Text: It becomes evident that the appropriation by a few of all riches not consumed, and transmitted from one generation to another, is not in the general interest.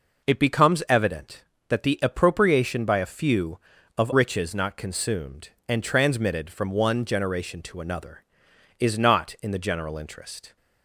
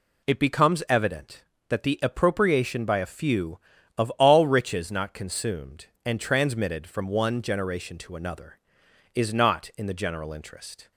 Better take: second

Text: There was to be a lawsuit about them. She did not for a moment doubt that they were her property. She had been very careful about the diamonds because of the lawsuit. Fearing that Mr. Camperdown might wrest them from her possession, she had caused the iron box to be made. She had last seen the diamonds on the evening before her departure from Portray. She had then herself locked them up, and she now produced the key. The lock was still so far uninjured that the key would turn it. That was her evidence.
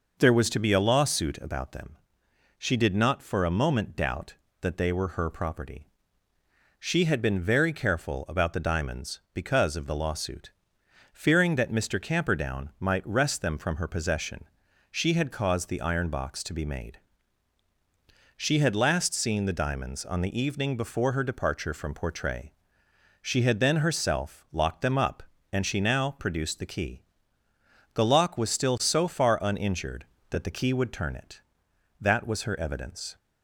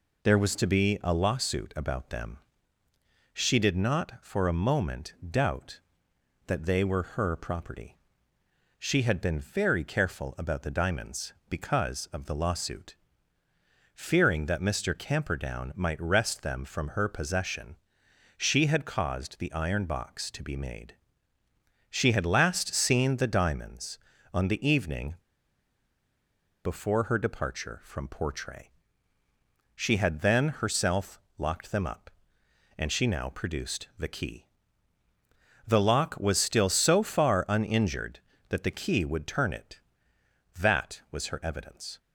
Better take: first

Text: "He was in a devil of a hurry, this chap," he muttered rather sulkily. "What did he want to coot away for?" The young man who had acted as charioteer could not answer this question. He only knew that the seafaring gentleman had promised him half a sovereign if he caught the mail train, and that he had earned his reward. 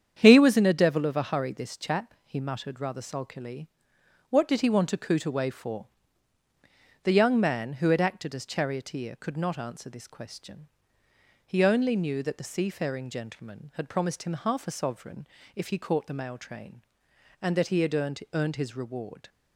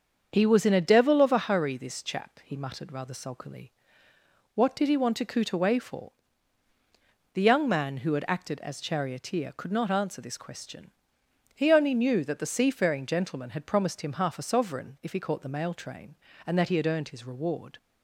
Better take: second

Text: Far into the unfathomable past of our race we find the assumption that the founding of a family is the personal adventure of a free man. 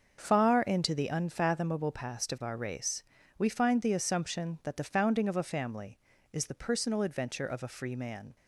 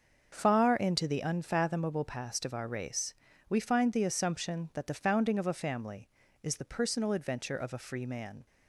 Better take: neither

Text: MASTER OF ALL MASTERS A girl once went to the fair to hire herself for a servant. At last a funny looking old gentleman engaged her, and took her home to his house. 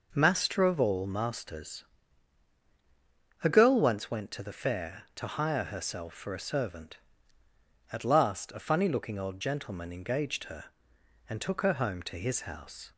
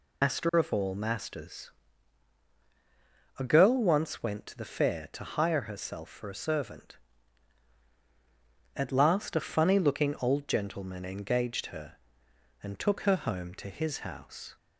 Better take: first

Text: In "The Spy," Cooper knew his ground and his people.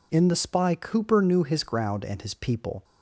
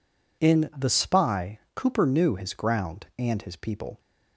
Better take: neither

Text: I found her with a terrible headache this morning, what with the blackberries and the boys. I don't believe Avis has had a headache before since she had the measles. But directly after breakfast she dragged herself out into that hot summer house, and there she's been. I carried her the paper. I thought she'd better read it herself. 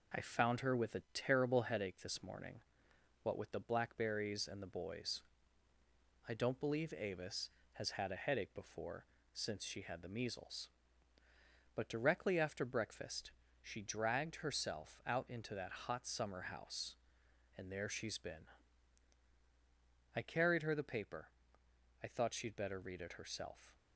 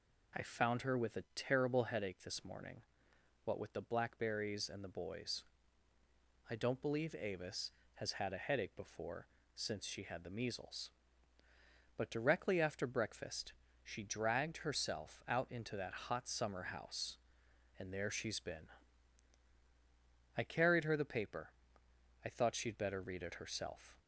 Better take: second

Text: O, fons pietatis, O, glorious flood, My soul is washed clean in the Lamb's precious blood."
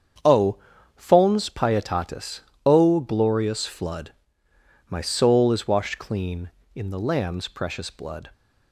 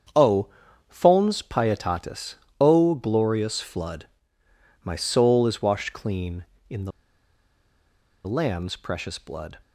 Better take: first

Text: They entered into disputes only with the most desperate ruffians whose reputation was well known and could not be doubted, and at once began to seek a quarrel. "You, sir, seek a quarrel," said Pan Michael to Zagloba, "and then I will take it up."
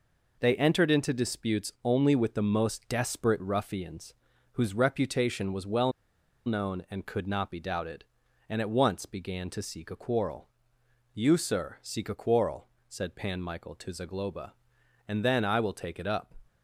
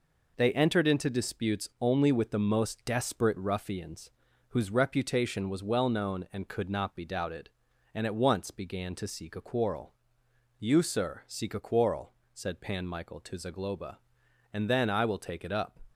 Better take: second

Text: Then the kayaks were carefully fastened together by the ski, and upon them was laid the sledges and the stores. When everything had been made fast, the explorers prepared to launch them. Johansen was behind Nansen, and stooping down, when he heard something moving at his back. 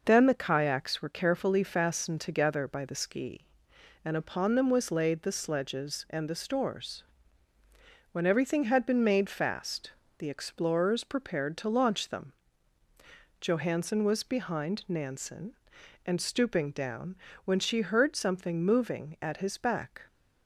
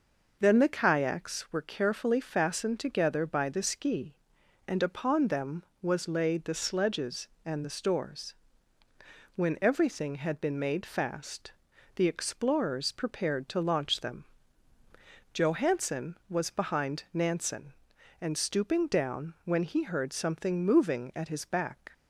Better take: second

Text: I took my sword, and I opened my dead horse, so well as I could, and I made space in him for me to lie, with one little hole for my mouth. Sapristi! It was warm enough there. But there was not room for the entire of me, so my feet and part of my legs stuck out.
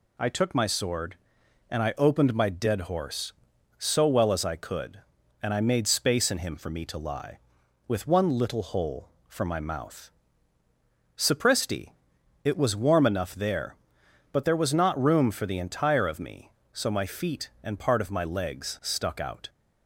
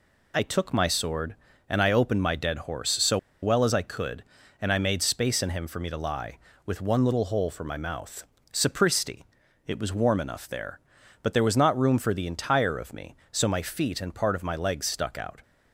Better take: first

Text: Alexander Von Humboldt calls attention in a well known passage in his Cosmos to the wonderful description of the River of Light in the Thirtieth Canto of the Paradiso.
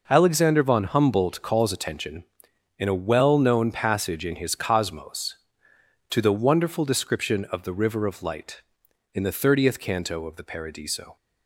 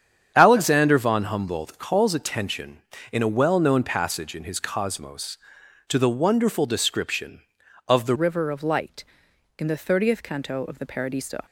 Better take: first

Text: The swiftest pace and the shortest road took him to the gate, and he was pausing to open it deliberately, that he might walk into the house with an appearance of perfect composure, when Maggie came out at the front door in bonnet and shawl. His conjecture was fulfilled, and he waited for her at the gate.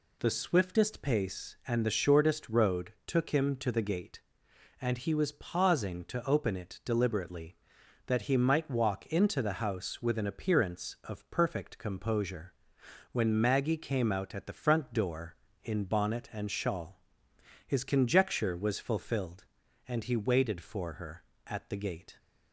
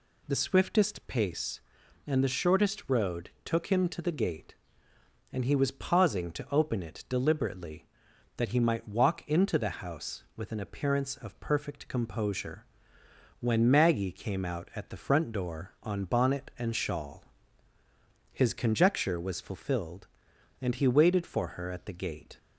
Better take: first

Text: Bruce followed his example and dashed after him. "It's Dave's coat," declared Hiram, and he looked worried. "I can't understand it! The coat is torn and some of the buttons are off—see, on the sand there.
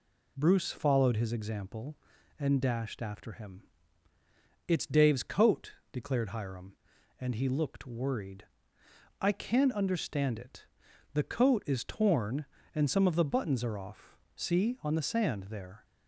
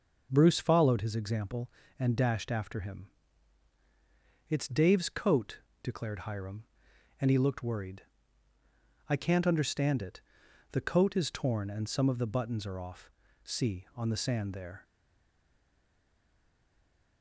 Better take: first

